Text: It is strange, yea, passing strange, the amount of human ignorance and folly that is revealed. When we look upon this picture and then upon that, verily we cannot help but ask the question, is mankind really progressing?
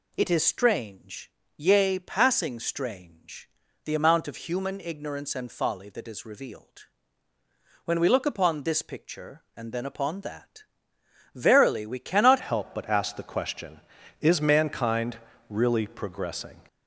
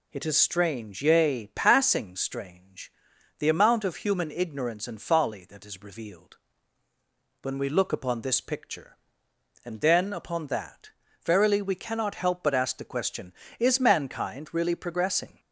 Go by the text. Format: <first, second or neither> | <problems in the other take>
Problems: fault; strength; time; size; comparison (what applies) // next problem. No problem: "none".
second | changes voice at "help"; from 12.4 s on; 4.1 s long // pauses between "mankind" and "really"; slight; at 15.1 s; 0.32 s long